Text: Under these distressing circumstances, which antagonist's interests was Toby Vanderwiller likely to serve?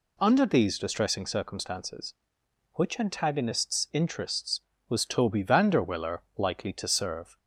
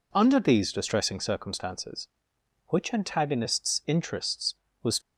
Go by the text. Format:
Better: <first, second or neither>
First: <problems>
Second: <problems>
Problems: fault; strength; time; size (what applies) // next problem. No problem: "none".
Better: first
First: none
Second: stops before "Toby Vanderwiller likely to serve"; at 5.0 s